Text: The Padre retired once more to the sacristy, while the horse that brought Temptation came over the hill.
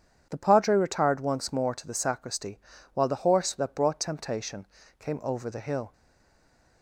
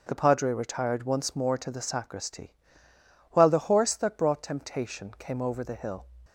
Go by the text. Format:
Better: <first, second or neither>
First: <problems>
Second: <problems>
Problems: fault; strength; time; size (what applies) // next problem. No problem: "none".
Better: second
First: pauses between "Temptation" and "came"; slight; at 4.6 s; 0.32 s long // stays silent after the last word; slight; from 5.9 s on; 0.9 s long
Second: none